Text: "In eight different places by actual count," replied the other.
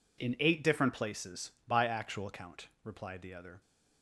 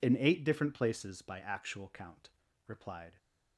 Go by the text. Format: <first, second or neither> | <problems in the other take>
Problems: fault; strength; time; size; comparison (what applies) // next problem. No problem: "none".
first | stops before "the other"; at 3.1 s